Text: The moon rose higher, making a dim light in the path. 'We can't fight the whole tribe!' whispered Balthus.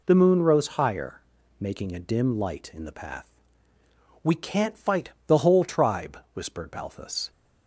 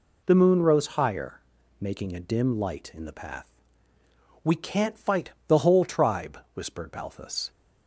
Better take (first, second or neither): neither